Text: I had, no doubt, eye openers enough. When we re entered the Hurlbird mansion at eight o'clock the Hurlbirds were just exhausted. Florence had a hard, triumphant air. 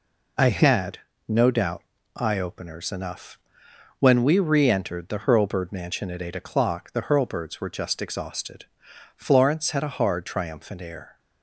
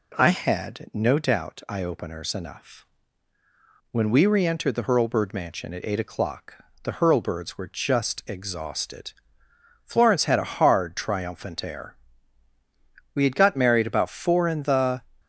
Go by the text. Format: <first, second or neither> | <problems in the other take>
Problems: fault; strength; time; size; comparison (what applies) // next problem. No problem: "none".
first | pauses between "o'clock" and "the"; slight; at 6.5 s; 0.28 s long // goes on to say "We had got married about four in the"; strong; from 13.1 s on; 1.8 s long